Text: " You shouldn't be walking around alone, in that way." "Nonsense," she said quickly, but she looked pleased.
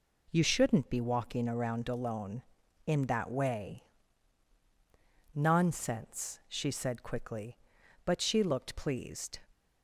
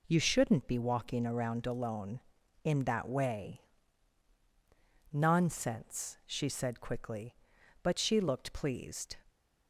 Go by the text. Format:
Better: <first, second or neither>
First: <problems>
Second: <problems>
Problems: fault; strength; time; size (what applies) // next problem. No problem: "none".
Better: neither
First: none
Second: none